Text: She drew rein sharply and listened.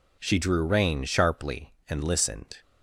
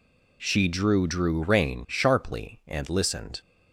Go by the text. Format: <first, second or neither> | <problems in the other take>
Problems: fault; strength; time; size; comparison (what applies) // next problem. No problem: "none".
first | says "drew" twice; at 1.0 s